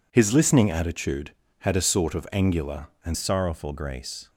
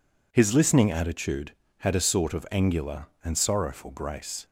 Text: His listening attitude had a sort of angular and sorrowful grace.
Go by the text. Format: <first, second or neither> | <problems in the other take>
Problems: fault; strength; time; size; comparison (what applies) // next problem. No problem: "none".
second | changes voice at "sorrowful"; from 3.1 s on; 1.1 s long